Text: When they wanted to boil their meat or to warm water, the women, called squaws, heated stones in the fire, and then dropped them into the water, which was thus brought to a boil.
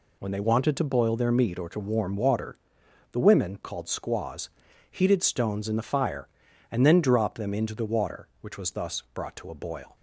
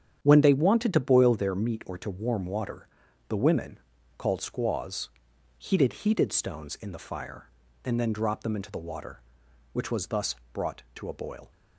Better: first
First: none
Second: starts louder than the rest; strong; until 1.2 s; 8.5 dB // says "heated" twice; at 5.9 s // pauses between "thus" and "brought"; slight; at 10.3 s; 0.18 s long

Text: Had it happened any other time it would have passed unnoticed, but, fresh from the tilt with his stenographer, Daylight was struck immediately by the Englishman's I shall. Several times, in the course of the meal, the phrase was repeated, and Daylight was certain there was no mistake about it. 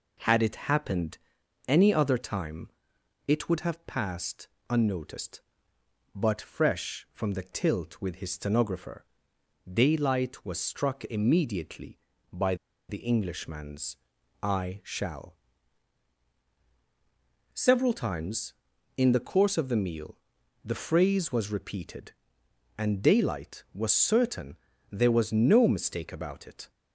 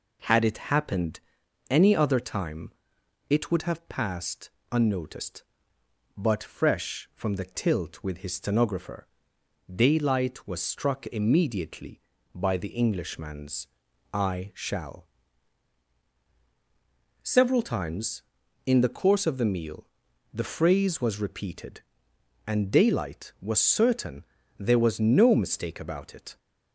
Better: second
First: pauses between "happened" and "any"; noticeable; at 1.1 s; 0.50 s long // pauses between "time" and "it"; noticeable; at 2.6 s; 0.58 s long // pauses between "passed" and "unnoticed"; slight; at 4.4 s; 0.22 s long // pauses between "by" and "the"; slight; at 12.5 s; 0.34 s long // pauses between "Englishman's" and "I"; noticeable; at 13.9 s; 0.46 s long // pauses between "certain" and "there"; slight; at 24.5 s; 0.34 s long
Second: pauses between "happened" and "any"; noticeable; at 1.1 s; 0.50 s long // pauses between "time" and "it"; noticeable; at 2.7 s; 0.58 s long // pauses between "passed" and "unnoticed"; slight; at 4.5 s; 0.22 s long // pauses between "Englishman's" and "I"; noticeable; at 13.6 s; 0.46 s long // pauses between "certain" and "there"; slight; at 24.2 s; 0.34 s long

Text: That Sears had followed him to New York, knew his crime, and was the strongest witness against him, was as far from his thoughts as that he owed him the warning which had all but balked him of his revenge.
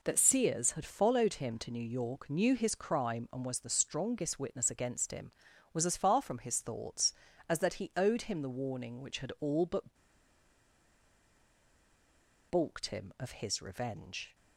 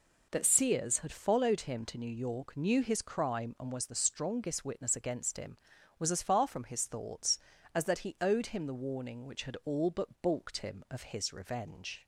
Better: second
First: pauses between "but" and "balked"; strong; at 9.9 s; 2.5 s long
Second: none

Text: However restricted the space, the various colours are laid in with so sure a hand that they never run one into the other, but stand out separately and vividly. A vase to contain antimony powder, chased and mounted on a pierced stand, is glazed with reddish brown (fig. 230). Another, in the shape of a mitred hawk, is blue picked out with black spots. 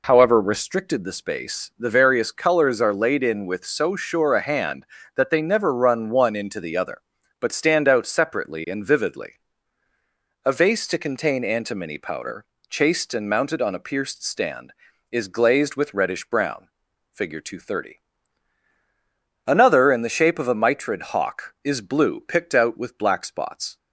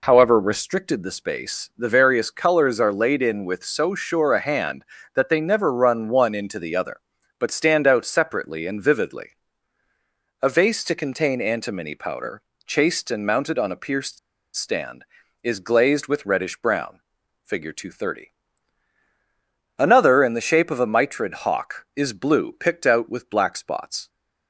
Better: first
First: none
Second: pauses between "pierced" and "stand"; at 14.1 s; 0.37 s long

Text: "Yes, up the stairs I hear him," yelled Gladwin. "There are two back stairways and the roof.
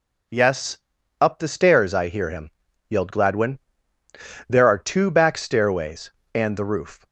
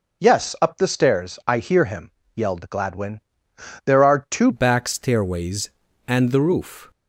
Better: first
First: none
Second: changes voice at "back"; from 4.5 s on; 2.4 s long

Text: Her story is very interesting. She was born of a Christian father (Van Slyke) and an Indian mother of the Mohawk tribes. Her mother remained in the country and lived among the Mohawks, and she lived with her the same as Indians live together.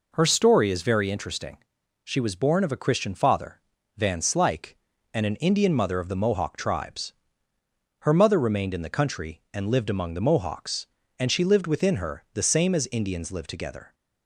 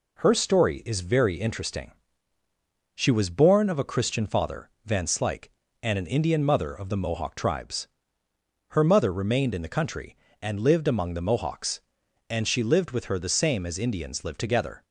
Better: second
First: says "within" for "with"; at 11.6 s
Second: none

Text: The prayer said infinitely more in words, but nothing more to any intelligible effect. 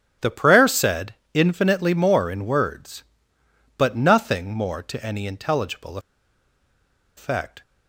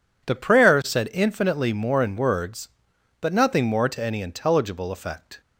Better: second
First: starts louder than the rest; strong; until 1.4 s; 10.5 dB // pauses between "said" and "infinitely"; slight; at 1.1 s; 0.20 s long // pauses between "intelligible" and "effect"; at 5.9 s; 1.1 s long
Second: none

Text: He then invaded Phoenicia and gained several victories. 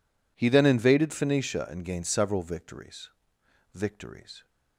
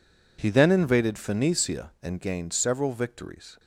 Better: second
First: says "victories" twice; at 3.7 s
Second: none

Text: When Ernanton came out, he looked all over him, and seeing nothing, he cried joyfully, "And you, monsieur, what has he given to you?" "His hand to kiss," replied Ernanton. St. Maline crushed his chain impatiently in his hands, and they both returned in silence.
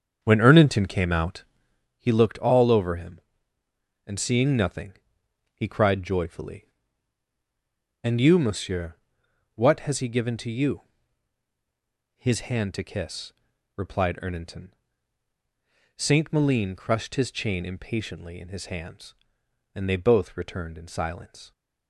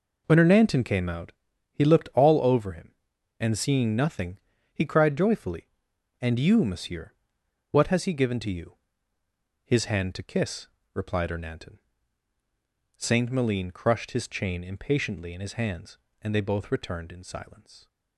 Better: second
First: starts louder than the rest; strong; until 1.9 s; 7 dB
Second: none

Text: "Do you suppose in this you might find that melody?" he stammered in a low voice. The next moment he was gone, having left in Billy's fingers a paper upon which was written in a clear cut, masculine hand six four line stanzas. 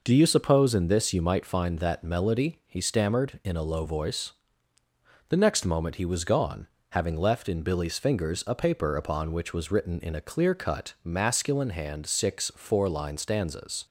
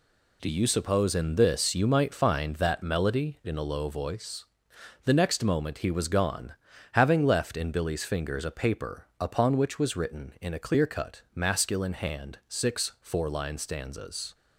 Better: first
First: none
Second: skips "he stammered"; at 3.4 s

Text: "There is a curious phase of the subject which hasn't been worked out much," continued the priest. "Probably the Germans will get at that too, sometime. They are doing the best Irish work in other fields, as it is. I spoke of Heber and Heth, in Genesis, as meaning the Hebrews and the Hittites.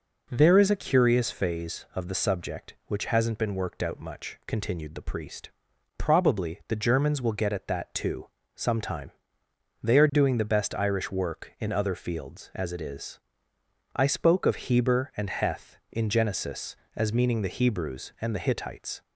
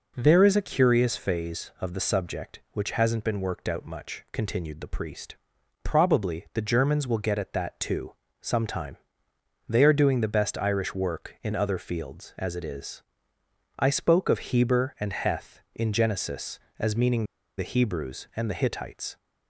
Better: first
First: none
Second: pauses between "meaning" and "the"; slight; at 17.2 s; 0.33 s long

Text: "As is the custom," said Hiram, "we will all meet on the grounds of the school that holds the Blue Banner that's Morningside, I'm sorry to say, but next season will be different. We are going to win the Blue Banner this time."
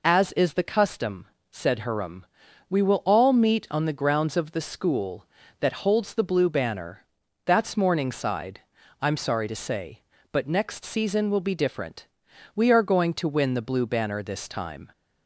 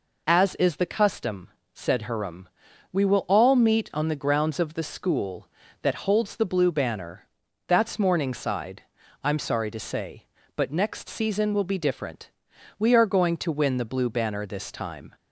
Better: neither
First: pauses between "Banner" and "that's"; at 7.0 s; 0.40 s long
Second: pauses between "Banner" and "that's"; at 7.2 s; 0.40 s long

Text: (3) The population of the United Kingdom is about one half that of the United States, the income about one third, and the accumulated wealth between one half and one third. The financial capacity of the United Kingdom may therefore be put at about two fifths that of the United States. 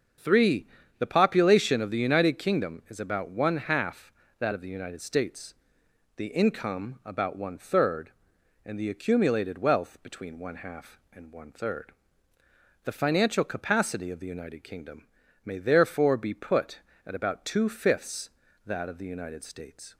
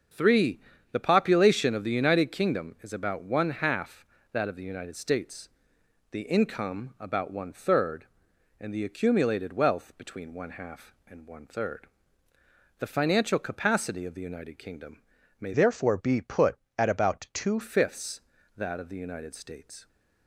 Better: first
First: starts louder than the rest; until 1.4 s; 6.5 dB // pauses between "Kingdom" and "may"; at 15.0 s; 0.41 s long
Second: starts louder than the rest; until 1.4 s; 6.5 dB // pauses between "Kingdom" and "may"; at 14.9 s; 0.42 s long // changes voice from "therefore" to "two"; from 15.5 to 17.5 s; 2.0 s long

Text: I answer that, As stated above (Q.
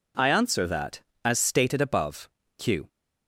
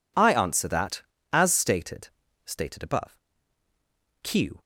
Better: first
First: none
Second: says "stated" twice; at 2.4 s

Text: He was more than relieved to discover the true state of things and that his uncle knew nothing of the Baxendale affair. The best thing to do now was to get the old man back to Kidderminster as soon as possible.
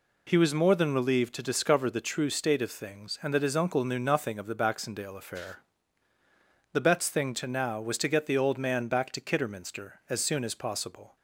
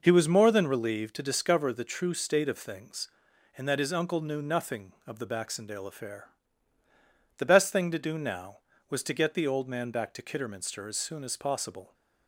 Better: second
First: skips "do"; at 7.4 s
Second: none

